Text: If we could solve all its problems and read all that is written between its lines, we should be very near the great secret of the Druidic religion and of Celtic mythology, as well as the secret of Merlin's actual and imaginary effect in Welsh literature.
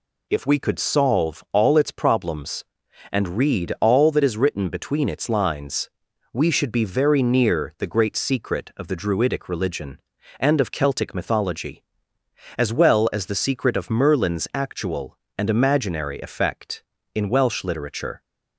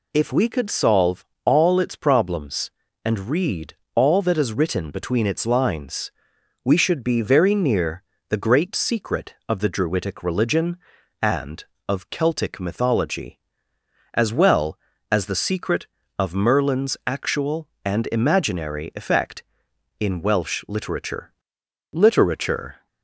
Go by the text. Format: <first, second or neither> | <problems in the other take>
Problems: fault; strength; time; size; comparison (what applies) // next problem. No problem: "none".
first | pauses between "solve" and "all"; slight; at 1.2 s; 0.18 s long // pauses between "read" and "all"; slight; at 3.7 s; 0.20 s long // pauses between "near" and "the"; slight; at 8.0 s; 0.24 s long // says "literature" twice; at 21.9 s